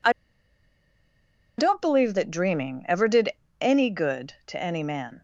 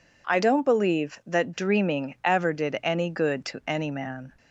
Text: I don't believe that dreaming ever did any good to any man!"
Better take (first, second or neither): second